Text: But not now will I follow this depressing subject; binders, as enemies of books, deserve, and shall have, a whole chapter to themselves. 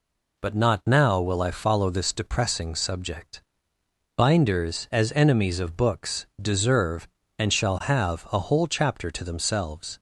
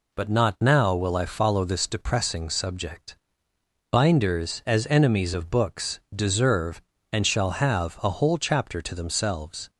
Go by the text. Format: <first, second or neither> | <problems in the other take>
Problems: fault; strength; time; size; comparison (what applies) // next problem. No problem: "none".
neither | none